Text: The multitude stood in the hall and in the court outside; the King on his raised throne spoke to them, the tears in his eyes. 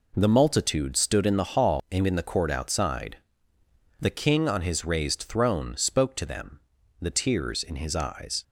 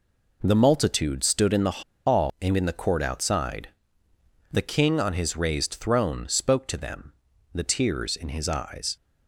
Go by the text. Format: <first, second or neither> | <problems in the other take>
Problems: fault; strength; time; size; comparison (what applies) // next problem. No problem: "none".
first | pauses between "the" and "hall"; slight; at 1.8 s; 0.23 s long